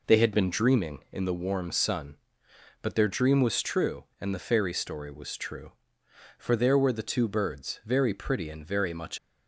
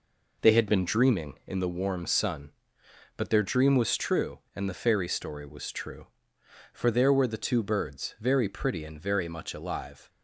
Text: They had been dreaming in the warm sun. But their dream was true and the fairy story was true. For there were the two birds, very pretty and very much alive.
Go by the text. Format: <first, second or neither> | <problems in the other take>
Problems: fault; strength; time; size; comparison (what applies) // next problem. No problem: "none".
second | stops before "alive"; at 9.1 s